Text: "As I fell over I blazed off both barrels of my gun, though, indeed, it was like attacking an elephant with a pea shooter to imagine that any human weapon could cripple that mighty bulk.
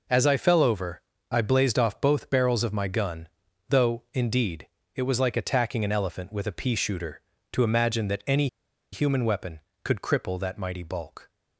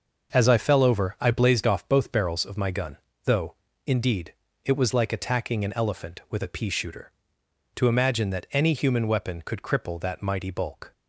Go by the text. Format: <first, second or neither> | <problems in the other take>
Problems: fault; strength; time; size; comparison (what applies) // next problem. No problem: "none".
second | pauses between "over" and "I"; slight; at 1.0 s; 0.30 s long // pauses between "any" and "human"; at 8.4 s; 0.45 s long